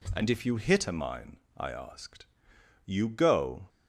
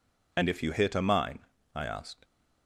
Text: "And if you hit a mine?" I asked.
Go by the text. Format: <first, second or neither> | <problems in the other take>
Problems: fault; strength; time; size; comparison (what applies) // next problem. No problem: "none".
second | goes on to say "You go"; noticeable; from 2.8 s on; 0.84 s long